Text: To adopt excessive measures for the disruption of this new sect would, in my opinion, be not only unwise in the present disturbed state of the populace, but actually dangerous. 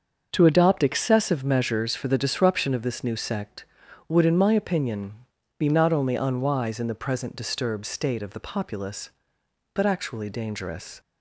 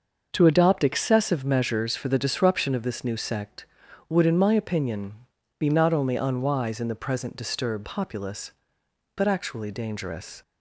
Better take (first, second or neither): first